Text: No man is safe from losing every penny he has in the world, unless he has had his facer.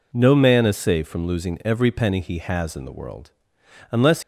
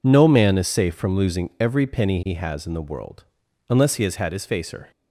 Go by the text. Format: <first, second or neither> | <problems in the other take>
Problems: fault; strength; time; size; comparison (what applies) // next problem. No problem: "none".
second | stops before "he has had his facer"; at 4.2 s